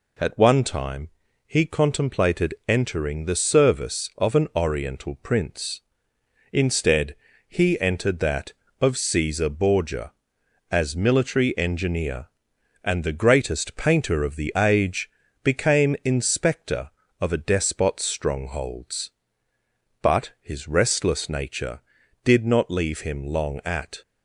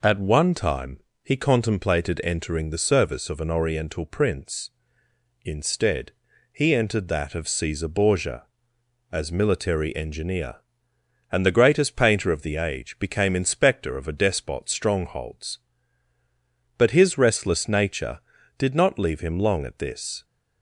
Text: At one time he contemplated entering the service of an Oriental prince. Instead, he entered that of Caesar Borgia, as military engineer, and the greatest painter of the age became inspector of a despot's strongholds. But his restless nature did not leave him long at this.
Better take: second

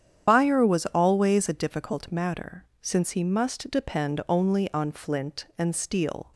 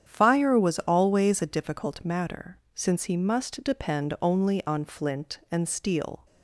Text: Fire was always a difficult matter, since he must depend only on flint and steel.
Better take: second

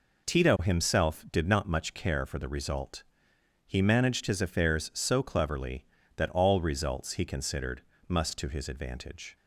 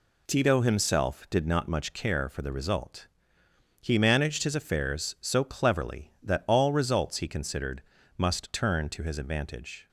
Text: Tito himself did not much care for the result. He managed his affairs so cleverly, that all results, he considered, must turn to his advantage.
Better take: second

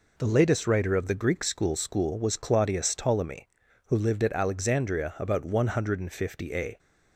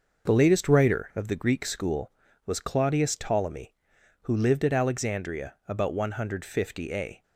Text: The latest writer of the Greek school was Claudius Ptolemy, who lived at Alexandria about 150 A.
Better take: second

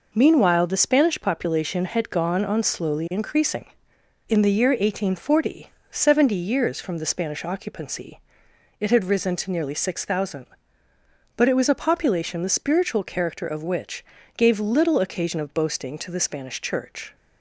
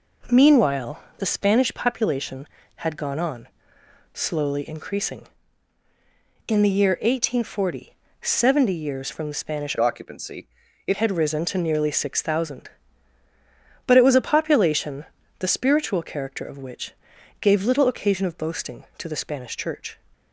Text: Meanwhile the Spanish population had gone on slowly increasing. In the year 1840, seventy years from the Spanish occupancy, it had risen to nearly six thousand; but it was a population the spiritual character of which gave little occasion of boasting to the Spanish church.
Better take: first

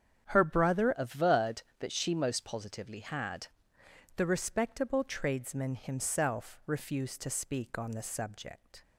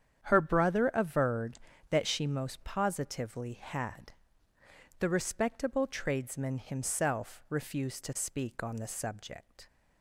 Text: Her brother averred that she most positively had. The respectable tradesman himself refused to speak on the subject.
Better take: second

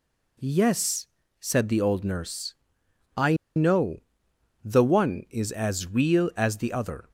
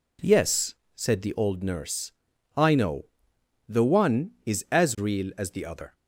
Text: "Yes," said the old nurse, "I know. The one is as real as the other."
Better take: second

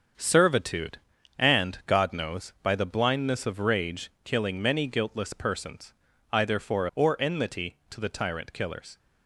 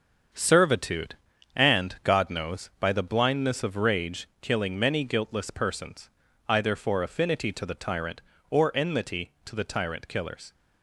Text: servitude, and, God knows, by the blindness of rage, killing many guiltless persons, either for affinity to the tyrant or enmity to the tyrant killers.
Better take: second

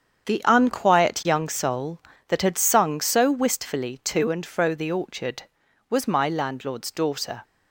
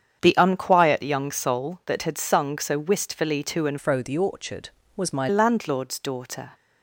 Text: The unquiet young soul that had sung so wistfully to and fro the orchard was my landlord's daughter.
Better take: first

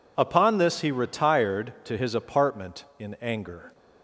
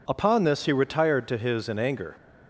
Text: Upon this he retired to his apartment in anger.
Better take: first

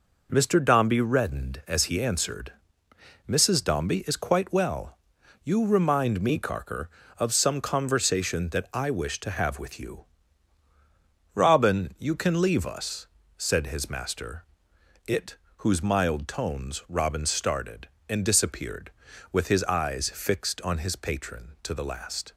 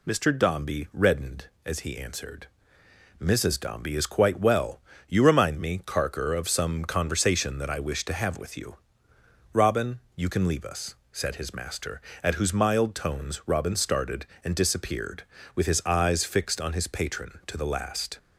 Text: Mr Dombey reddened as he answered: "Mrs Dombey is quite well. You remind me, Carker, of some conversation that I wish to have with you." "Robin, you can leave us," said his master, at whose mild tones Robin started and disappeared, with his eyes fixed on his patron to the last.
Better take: second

